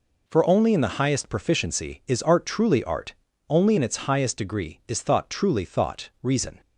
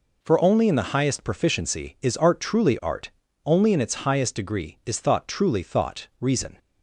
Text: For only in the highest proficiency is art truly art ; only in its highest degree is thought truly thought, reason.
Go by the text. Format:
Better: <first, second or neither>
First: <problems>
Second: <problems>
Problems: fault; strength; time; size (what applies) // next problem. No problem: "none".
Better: neither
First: none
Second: none